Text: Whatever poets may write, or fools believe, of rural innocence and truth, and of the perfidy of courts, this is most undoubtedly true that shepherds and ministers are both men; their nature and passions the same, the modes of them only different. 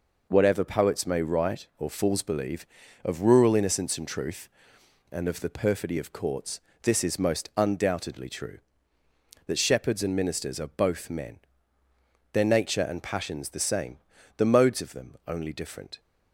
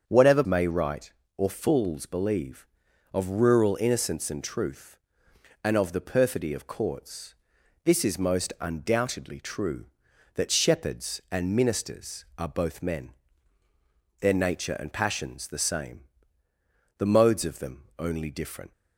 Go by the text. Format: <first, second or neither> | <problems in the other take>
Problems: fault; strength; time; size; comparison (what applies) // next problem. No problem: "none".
first | starts louder than the rest; until 1.1 s; 7 dB // skips "poets"; at 0.4 s // pauses between "them" and "only"; slight; at 17.8 s; 0.16 s long